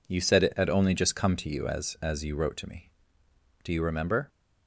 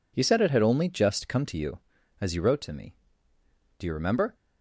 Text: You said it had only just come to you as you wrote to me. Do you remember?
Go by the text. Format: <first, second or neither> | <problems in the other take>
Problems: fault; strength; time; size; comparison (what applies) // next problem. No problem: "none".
second | says "as" twice; at 2.0 s